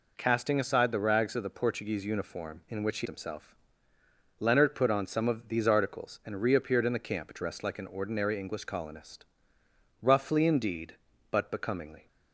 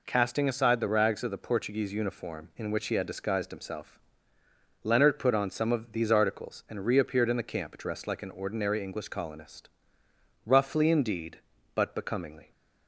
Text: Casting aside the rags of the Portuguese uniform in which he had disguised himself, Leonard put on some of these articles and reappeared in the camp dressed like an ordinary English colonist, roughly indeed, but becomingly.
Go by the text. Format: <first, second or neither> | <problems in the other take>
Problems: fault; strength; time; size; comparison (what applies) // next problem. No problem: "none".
second | skips "had disguised"; at 3.0 s